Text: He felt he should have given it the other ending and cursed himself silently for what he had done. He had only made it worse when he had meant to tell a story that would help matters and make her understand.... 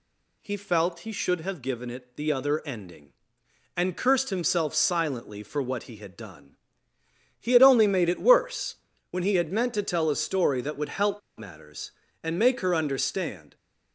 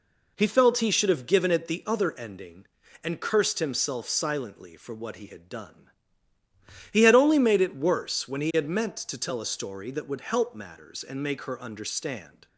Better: second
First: pauses between "worse" and "when"; slight; at 8.7 s; 0.34 s long // pauses between "help" and "matters"; slight; at 11.2 s; 0.19 s long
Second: none

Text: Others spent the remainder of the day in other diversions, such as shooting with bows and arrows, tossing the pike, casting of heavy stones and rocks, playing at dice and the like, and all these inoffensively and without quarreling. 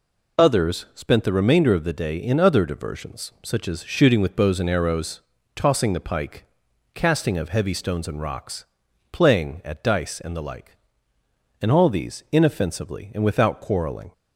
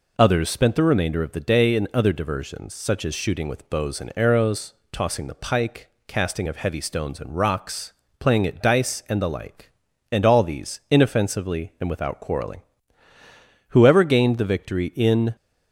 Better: first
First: none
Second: goes on to say "Whoever gained the victory in"; from 13.6 s on; 1.6 s long

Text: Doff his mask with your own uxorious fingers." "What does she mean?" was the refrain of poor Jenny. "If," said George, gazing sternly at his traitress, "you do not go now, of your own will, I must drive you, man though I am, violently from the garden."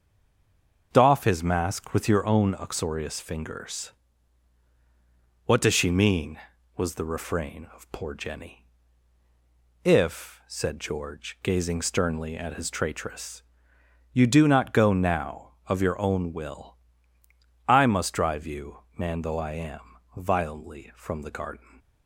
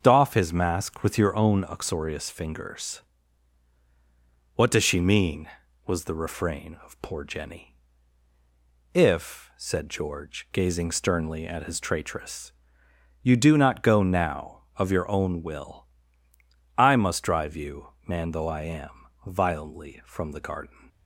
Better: second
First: stays silent before the first word; slight; until 0.9 s; 0.9 s long // starts louder than the rest; until 1.9 s; 6 dB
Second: starts louder than the rest; until 1.0 s; 6 dB

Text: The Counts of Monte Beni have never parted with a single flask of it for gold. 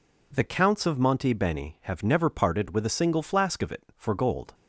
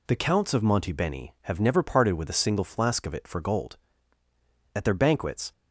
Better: first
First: none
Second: goes on to say "At their banquets"; noticeable; from 4.7 s on; 0.76 s long

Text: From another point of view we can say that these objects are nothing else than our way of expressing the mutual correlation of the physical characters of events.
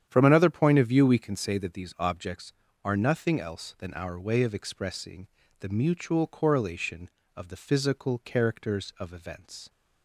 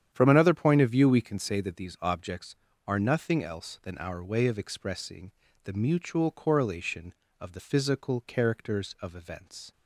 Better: neither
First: starts louder than the rest; strong; until 1.0 s; 9.5 dB // pauses between "expressing" and "the"; slight; at 5.2 s; 0.32 s long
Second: starts louder than the rest; strong; until 1.1 s; 9.5 dB // pauses between "expressing" and "the"; slight; at 5.3 s; 0.32 s long

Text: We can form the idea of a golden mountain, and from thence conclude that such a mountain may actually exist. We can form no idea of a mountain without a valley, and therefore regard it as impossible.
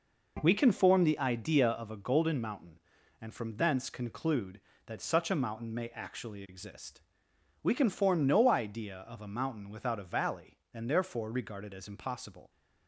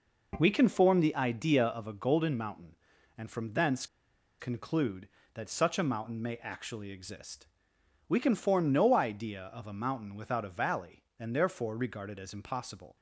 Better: first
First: none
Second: pauses between "thence" and "conclude"; noticeable; at 3.8 s; 0.53 s long

